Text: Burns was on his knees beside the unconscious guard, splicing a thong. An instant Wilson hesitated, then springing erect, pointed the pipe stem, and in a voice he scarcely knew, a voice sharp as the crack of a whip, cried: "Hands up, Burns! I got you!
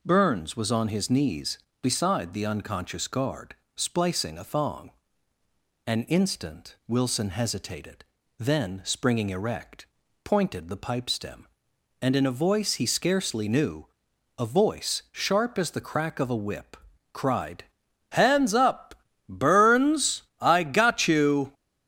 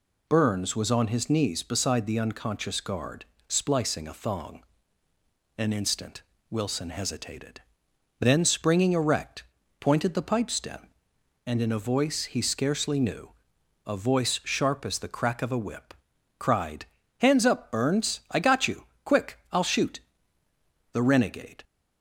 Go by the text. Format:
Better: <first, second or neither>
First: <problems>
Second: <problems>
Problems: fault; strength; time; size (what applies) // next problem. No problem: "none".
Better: first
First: none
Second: pauses between "instant" and "Wilson"; slight; at 6.2 s; 0.28 s long // goes on to say "Quick I'll shoot The renegade"; strong; from 19.0 s on; 2.6 s long